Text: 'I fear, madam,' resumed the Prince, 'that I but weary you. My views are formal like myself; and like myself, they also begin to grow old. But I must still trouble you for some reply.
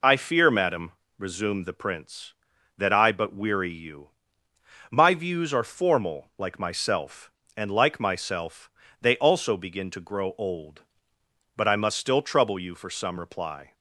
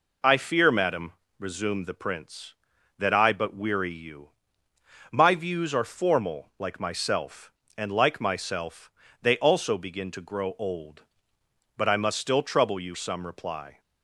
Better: first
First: none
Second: skips "for"; at 12.9 s

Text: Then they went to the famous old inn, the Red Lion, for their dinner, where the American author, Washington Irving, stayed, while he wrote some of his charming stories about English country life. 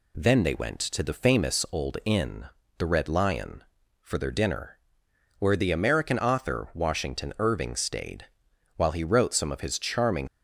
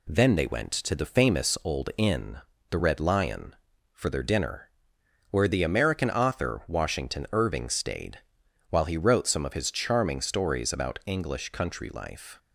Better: second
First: stops before "stories about English country life"; at 10.2 s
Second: none

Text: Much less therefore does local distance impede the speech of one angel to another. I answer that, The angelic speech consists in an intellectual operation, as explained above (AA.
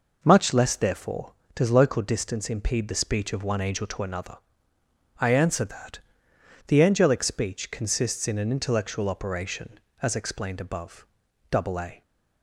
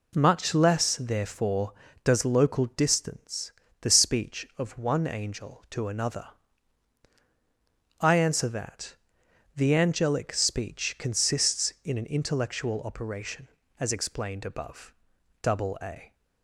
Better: first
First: none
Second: skips "impede"; at 3.6 s

